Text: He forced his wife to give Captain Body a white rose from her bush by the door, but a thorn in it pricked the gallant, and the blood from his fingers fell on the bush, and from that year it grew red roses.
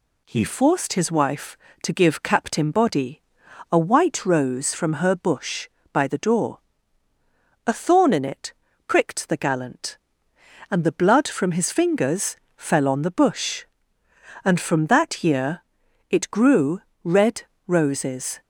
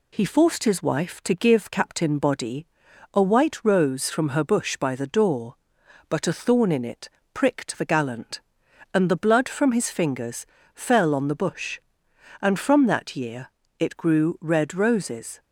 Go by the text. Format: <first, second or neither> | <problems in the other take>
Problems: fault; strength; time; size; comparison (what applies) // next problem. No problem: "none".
second | pauses between "Body" and "a"; noticeable; at 3.2 s; 0.50 s long; noticeable in the second // skips "but"; at 7.1 s // pauses between "it" and "pricked"; slight; at 8.5 s; 0.34 s long; slight in the second // pauses between "fingers" and "fell"; slight; at 12.3 s; 0.20 s long; slight in the second // pauses between "year" and "it"; noticeable; at 15.6 s; 0.48 s long; slight in the second // pauses between "grew" and "red"; slight; at 16.8 s; 0.24 s long // pauses between "red" and "roses"; slight; at 17.4 s; 0.24 s long